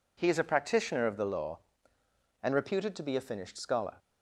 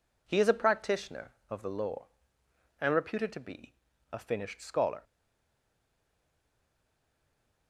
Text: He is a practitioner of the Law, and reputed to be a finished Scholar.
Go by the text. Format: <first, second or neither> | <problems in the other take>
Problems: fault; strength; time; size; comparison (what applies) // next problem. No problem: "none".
first | pauses between "be" and "a"; slight; at 3.7 s; 0.36 s long // stays silent after the last word; strong; from 5.0 s on; 2.6 s long